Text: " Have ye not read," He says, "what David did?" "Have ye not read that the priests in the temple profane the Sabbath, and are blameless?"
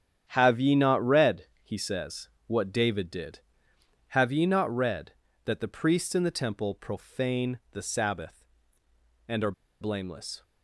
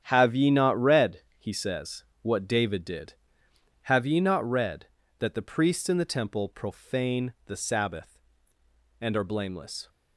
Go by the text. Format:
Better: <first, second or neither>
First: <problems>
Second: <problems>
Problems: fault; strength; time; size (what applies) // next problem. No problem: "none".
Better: second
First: starts louder than the rest; strong; until 1.3 s; 9 dB // pauses between "are" and "blameless"; slight; at 9.5 s; 0.29 s long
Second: starts louder than the rest; strong; until 1.0 s; 9 dB